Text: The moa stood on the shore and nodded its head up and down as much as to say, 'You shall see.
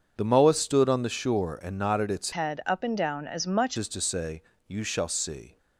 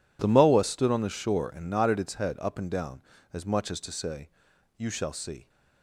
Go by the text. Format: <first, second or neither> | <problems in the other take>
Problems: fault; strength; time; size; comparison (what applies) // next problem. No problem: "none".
second | starts louder than the rest; until 1.1 s; 7 dB // changes voice from "head" to "much"; from 2.3 to 3.7 s; 1.4 s long